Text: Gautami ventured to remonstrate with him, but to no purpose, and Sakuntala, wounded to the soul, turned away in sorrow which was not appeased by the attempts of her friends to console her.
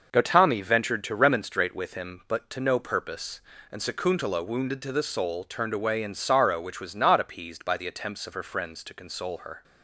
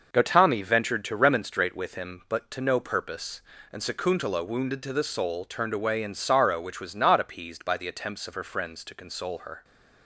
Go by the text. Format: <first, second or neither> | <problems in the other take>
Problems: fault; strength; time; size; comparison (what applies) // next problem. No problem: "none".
neither | none